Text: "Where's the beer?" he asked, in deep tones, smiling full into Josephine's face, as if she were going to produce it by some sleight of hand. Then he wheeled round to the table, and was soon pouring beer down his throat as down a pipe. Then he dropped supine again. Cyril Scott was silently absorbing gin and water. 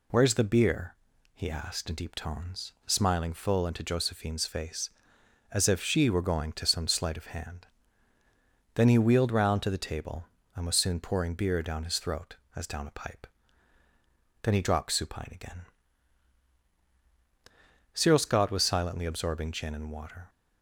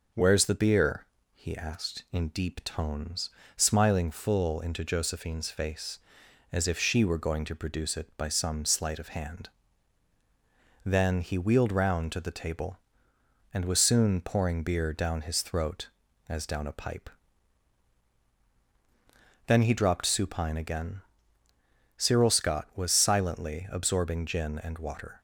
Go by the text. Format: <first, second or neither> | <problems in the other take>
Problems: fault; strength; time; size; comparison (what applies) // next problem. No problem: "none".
second | skips "produce it by"; at 6.6 s